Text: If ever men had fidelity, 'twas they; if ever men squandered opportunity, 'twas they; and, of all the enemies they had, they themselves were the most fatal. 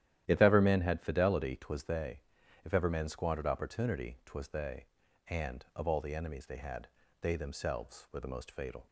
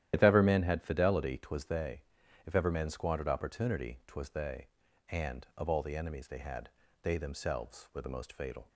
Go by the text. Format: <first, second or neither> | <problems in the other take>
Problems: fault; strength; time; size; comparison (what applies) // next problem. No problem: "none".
first | loses the start of "If"; at 0.1 s; 50 ms // starts louder than the rest; strong; until 1.1 s; 11.5 dB; strong in the first